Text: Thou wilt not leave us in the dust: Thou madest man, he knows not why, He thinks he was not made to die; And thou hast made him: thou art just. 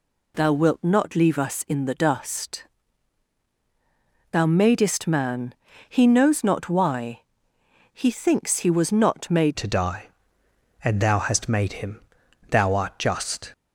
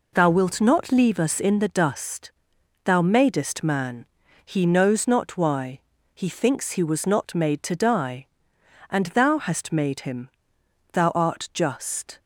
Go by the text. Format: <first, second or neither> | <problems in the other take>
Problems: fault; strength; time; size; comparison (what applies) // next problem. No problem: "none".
second | changes voice at "to"; from 9.5 s on; 4.0 s long